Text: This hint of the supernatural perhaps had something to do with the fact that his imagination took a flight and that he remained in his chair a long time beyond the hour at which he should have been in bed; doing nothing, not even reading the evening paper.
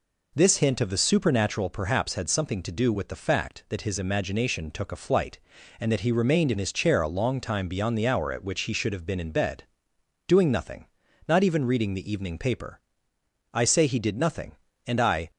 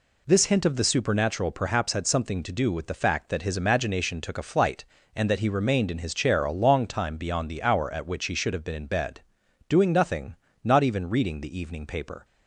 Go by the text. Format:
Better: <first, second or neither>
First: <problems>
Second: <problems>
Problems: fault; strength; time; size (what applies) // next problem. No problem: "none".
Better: second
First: goes on to say "I say he did nothing and I"; strong; from 13.5 s on; 1.7 s long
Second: none